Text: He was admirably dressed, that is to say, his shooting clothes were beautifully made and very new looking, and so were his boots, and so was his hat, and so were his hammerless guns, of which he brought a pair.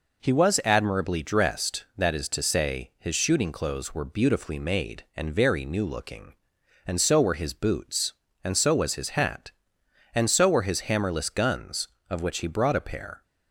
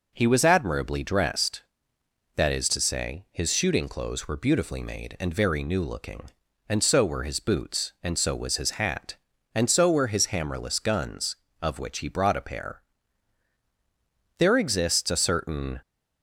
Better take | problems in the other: first | goes on to say "There exists a certain"; from 14.3 s on; 1.4 s long

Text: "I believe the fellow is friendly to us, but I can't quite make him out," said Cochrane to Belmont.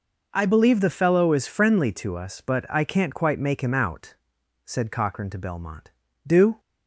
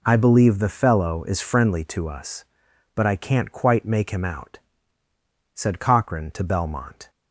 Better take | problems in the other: second | goes on to say "Do"; slight; from 6.2 s on; 0.36 s long

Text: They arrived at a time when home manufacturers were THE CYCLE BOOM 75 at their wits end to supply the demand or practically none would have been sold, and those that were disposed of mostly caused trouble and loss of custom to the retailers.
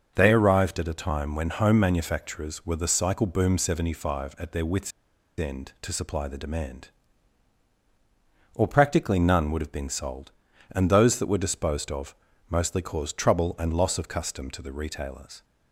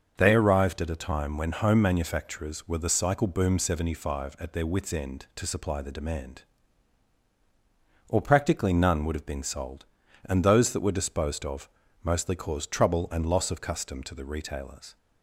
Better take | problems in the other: second | starts louder than the rest; until 1.1 s; 6.5 dB; also in the second // pauses between "wits" and "end"; noticeable; at 4.9 s; 0.47 s long // pauses between "of" and "mostly"; slight; at 12.1 s; 0.32 s long; slight in the second

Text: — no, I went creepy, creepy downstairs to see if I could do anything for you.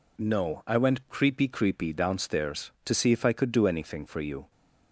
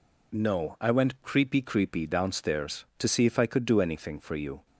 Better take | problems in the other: neither | none

